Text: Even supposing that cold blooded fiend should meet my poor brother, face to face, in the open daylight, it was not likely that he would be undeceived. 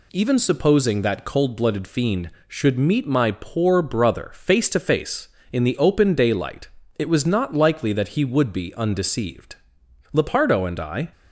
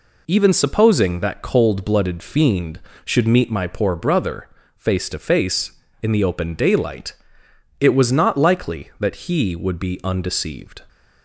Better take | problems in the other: second | goes on to say "Lepardo and I"; noticeable; from 10.1 s on; 0.98 s long

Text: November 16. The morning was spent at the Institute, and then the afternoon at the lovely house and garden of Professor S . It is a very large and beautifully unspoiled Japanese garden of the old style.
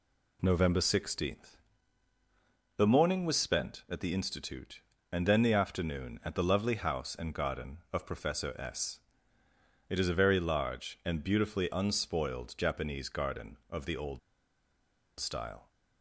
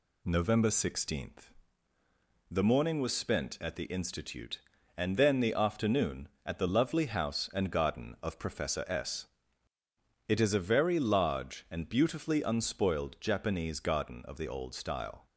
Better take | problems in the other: second | pauses between "old" and "style"; at 14.1 s; 1.0 s long

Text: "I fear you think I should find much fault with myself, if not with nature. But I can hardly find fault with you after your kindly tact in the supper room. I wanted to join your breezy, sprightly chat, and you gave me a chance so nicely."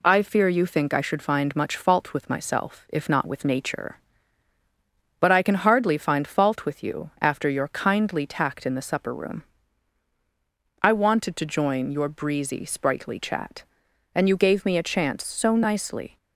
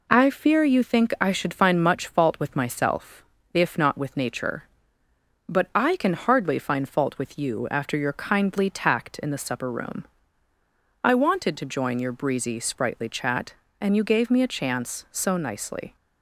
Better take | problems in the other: neither | none

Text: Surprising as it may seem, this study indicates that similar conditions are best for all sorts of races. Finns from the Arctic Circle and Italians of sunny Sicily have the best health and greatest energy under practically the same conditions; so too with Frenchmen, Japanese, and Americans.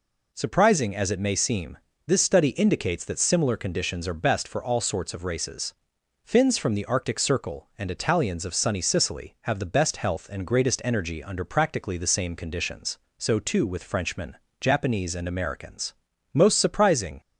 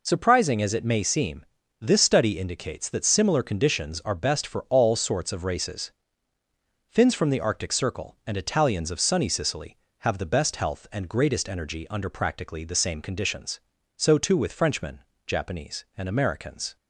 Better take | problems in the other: second | goes on to say "Most surprising"; noticeable; from 16.3 s on; 0.88 s long

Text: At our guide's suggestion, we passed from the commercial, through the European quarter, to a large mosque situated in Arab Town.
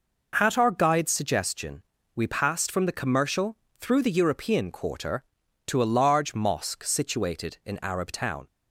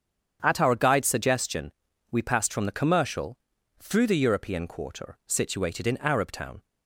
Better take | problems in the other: first | starts louder than the rest; strong; until 1.4 s; 8 dB // skips "to a large mosque"; at 5.2 s

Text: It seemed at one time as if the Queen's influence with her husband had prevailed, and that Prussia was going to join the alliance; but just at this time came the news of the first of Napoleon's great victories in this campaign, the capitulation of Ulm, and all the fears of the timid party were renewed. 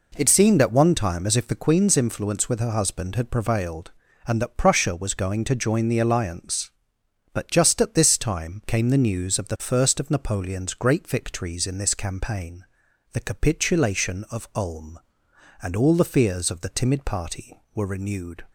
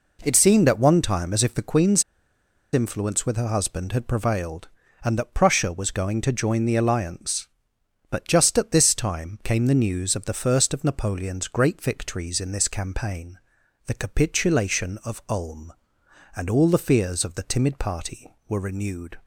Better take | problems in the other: first | pauses between "Queen's" and "influence"; noticeable; at 2.0 s; 0.71 s long

